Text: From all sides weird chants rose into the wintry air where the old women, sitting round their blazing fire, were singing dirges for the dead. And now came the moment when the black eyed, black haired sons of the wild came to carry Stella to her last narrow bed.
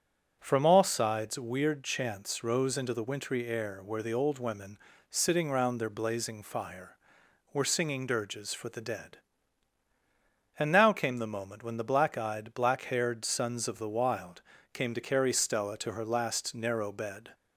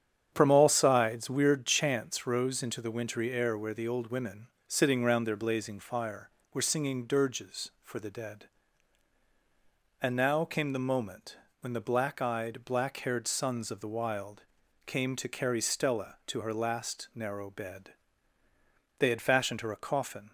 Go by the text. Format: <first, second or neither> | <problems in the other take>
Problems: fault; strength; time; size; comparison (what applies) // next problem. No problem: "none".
first | starts louder than the rest; strong; until 1.3 s; 8.5 dB; strong in the first // pauses between "moment" and "when"; slight; at 11.3 s; 0.22 s long // pauses between "wild" and "came"; noticeable; at 14.4 s; 0.46 s long; slight in the first // goes on to say "They had fashioned her a coffin"; from 18.9 s on; 1.3 s long